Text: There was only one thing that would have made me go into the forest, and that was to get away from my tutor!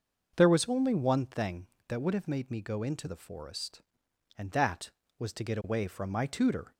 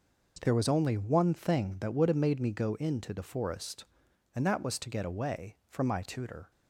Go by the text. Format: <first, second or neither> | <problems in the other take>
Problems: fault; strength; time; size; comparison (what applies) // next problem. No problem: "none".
neither | none